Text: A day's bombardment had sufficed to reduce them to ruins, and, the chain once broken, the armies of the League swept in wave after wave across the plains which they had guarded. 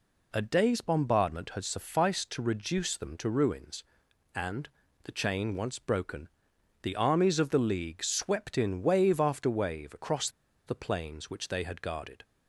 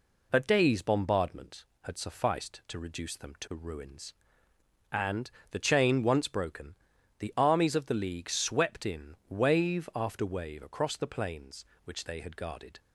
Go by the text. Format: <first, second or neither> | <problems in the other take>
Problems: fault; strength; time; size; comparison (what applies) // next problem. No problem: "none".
second | pauses between "across" and "the"; at 10.2 s; 0.38 s long